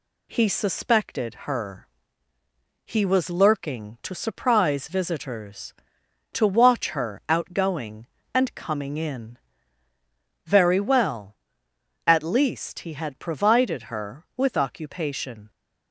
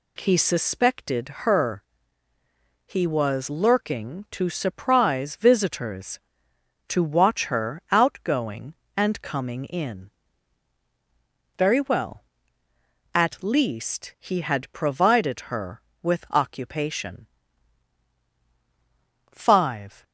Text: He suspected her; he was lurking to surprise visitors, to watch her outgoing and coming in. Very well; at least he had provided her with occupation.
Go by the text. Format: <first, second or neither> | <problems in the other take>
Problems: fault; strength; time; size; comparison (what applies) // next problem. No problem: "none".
first | pauses between "suspected" and "her"; slight; at 1.2 s; 0.16 s long // goes on to say "Five"; noticeable; from 19.3 s on; 0.72 s long